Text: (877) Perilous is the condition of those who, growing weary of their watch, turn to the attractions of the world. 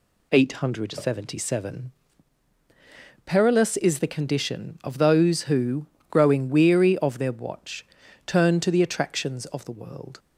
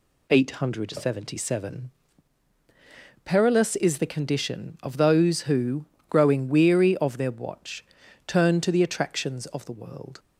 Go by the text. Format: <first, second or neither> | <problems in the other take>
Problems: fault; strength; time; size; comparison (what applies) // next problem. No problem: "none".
neither | none